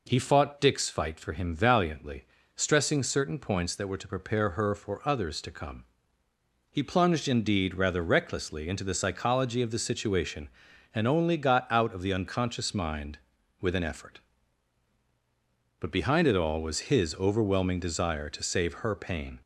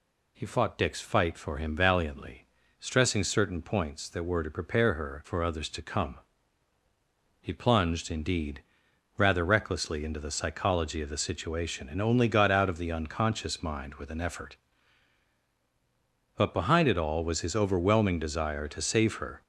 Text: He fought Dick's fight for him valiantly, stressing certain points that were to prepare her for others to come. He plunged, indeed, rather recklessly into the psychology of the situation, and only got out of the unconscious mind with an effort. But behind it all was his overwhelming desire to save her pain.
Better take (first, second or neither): first